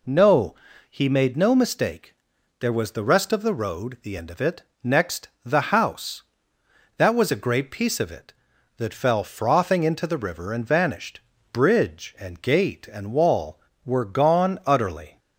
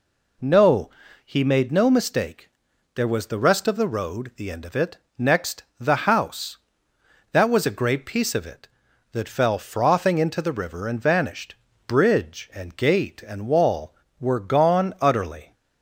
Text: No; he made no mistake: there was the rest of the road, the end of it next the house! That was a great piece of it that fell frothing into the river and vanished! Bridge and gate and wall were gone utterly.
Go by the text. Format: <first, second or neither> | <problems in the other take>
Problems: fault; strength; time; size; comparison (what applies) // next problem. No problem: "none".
neither | pauses between "it" and "next"; slight; the same in both // pauses between "next" and "the"; slight; the same in both